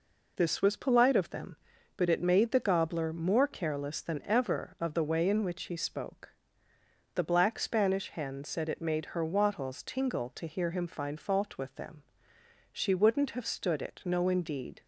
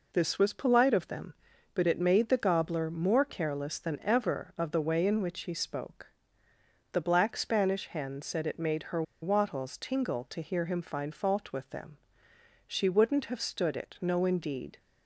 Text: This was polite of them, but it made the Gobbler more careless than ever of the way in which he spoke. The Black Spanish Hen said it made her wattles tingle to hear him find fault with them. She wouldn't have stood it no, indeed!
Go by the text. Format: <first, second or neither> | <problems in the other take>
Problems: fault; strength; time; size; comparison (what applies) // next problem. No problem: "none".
first | pauses between "her" and "wattles"; slight; at 9.0 s; 0.20 s long